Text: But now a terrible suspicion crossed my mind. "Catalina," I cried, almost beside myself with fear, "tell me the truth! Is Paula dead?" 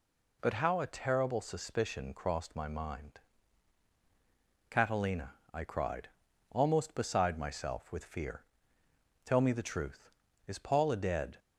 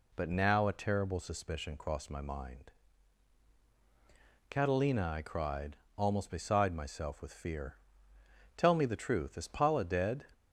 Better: second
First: says "how" for "now"; at 0.5 s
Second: none

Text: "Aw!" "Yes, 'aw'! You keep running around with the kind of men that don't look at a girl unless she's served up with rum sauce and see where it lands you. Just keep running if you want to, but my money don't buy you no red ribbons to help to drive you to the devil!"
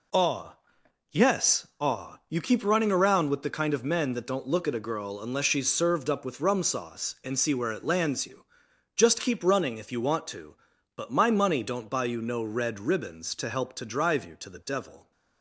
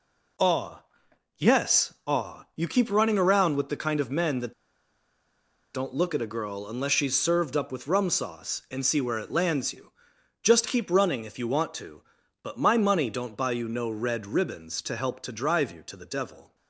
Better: first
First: none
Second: pauses between "that" and "don't"; at 4.5 s; 1.2 s long

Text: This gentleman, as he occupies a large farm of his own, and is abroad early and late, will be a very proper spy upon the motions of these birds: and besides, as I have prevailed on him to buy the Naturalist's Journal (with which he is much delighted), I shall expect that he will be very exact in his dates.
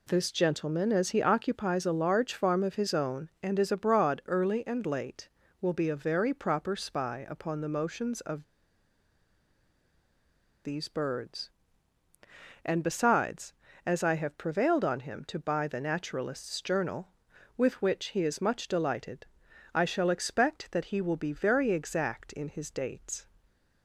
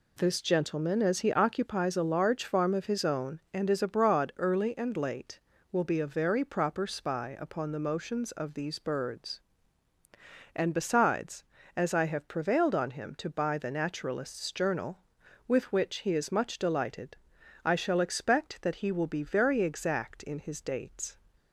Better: second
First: pauses between "of" and "these"; strong; at 8.4 s; 2.2 s long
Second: none

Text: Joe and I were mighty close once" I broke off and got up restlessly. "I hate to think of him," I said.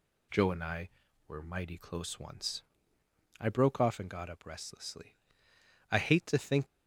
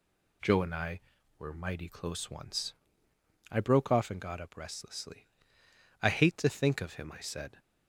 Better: second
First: pauses between "once" and "I"; noticeable; at 2.6 s; 0.78 s long // stops before "of him I said"; at 6.6 s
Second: pauses between "once" and "I"; noticeable; at 2.7 s; 0.78 s long

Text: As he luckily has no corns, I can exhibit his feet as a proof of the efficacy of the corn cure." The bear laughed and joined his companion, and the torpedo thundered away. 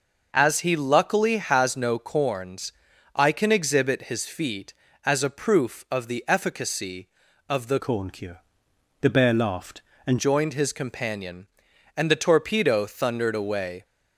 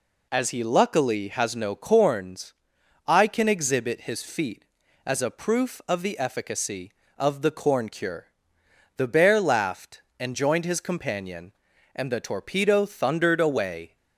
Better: second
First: changes voice from "corn" to "and"; from 7.7 to 10.1 s; 2.4 s long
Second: none

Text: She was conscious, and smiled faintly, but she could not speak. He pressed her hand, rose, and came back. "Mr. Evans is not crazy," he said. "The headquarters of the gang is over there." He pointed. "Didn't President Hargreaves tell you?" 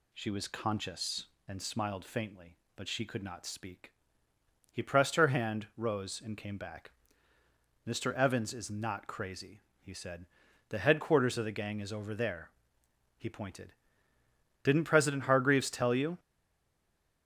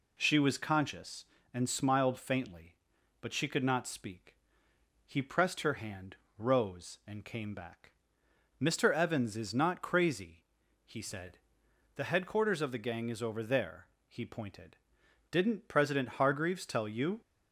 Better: second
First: stays silent after the last word; from 16.1 s on; 1.1 s long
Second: none

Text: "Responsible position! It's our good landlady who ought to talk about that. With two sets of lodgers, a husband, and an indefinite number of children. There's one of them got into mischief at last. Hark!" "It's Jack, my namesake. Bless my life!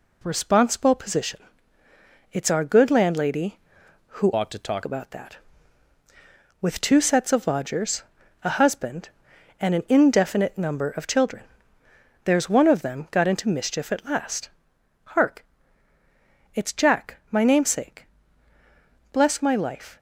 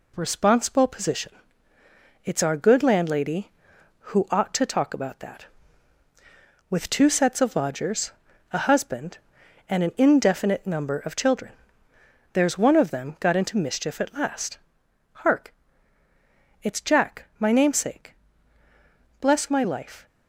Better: second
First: changes voice from "ought" to "talk"; from 4.3 to 4.8 s; 0.5 s long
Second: none

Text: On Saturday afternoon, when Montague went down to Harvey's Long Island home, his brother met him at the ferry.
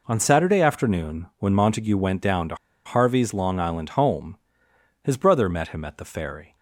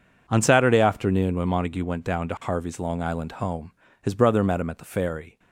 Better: second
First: pauses between "to" and "Harvey's"; slight; at 2.5 s; 0.29 s long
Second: none

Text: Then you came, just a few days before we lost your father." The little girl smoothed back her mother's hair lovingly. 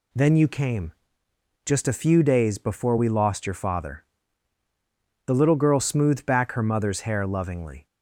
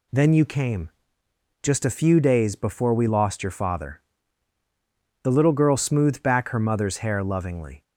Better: neither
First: none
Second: none

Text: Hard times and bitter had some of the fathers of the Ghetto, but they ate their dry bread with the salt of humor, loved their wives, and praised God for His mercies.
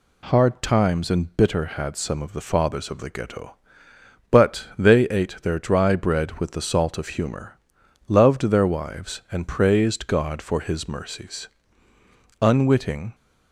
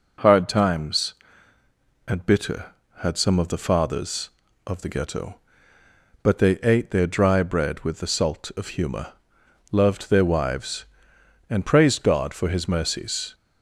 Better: second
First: goes on to say "Unwitting"; noticeable; from 12.3 s on; 0.76 s long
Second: none

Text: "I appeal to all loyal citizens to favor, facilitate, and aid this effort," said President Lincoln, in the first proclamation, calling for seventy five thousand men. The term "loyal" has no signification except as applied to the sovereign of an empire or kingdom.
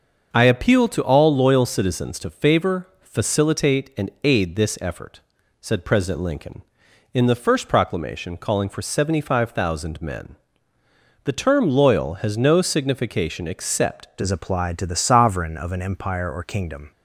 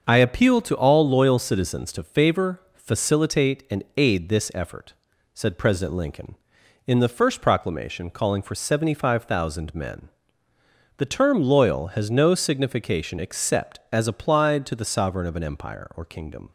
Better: second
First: starts louder than the rest; until 1.3 s; 6.5 dB // changes voice at "as"; from 14.2 s on; 2.7 s long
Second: starts louder than the rest; until 1.0 s; 6.5 dB

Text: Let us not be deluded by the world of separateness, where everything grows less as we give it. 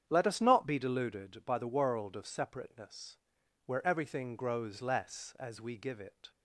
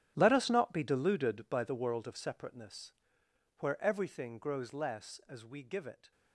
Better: first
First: starts louder than the rest; strong; until 1.0 s; 8.5 dB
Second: gets quieter; strong; throughout; 15 dB // starts louder than the rest; strong; until 1.1 s; 10 dB

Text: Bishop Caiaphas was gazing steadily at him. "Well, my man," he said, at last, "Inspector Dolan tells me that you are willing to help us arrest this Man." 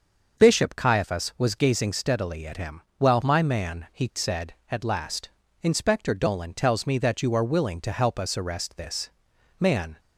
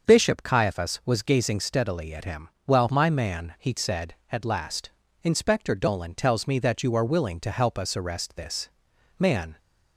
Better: neither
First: starts louder than the rest; until 1.4 s; 6 dB // pauses between "this" and "Man"; noticeable; at 9.0 s; 0.52 s long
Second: starts louder than the rest; until 1.1 s; 6 dB // pauses between "this" and "Man"; noticeable; at 8.6 s; 0.52 s long

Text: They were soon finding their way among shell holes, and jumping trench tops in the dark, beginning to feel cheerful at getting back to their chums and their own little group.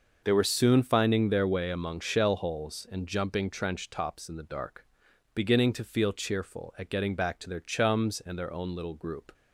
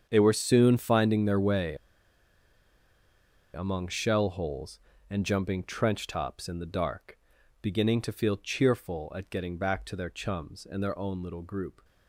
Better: first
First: starts louder than the rest; noticeable; until 1.2 s; 6 dB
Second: starts louder than the rest; strong; until 1.1 s; 7.5 dB // pauses between "way" and "among"; strong; at 1.7 s; 1.7 s long

